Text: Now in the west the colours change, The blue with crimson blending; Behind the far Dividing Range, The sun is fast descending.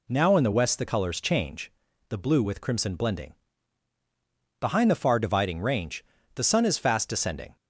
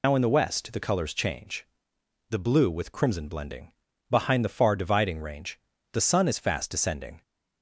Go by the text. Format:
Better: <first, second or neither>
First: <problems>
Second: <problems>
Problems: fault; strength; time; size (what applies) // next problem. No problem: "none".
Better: first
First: none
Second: loses the start of "Now"; at 0.0 s; 100 ms